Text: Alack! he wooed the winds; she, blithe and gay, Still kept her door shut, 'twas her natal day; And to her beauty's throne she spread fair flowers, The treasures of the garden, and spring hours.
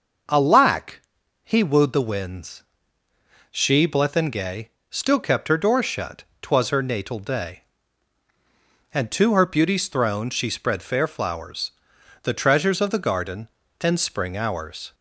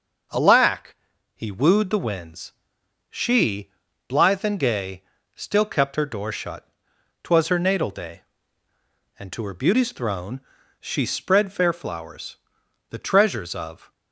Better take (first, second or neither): first